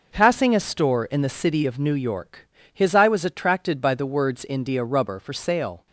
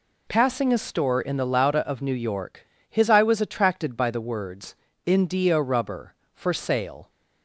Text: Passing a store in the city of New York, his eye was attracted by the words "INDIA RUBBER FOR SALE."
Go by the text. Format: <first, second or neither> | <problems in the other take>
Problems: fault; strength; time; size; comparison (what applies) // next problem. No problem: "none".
first | says "lauda" for "city"; at 1.4 s // pauses between "words" and "INDIA"; slight; at 4.7 s; 0.30 s long